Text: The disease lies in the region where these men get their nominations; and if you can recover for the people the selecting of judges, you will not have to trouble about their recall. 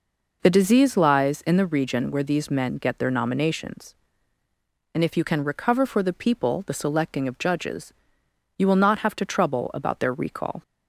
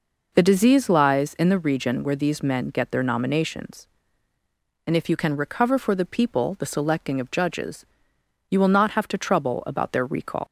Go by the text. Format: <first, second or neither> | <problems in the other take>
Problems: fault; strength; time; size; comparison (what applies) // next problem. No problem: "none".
first | leaves "recall" unfinished; at 10.4 s; 75 ms